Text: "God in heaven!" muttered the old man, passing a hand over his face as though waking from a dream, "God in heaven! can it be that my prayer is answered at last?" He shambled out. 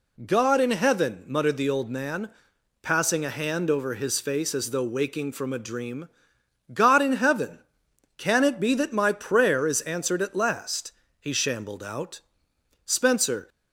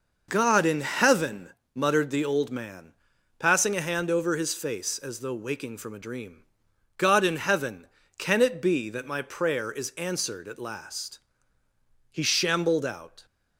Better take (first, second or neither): second